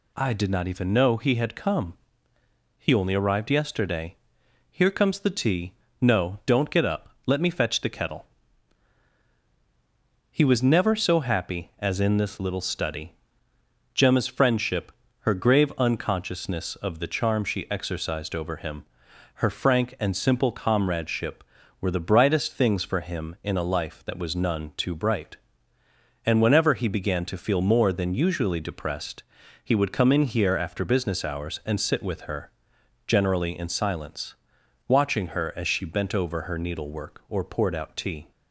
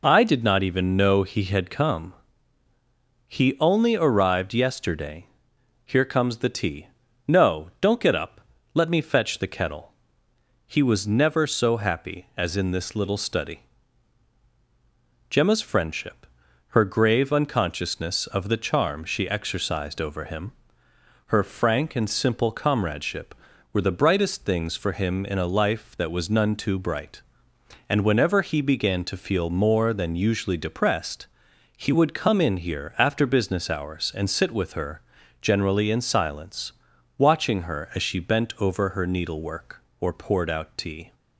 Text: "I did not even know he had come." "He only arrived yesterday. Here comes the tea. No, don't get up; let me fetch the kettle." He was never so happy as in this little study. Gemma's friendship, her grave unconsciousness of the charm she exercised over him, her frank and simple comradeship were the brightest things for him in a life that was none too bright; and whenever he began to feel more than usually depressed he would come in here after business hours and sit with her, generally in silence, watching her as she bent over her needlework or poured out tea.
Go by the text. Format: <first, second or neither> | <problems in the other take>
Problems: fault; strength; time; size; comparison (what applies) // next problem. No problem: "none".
neither | pauses between "depressed" and "he"; the same in both